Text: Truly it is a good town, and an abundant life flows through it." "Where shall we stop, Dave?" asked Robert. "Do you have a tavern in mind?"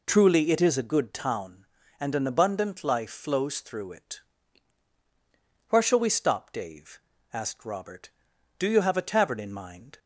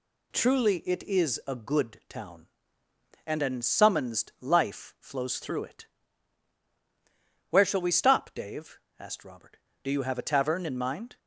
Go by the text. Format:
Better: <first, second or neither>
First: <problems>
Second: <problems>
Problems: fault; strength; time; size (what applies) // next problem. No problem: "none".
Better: first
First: none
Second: says "summonsed" for "abundant"; at 3.6 s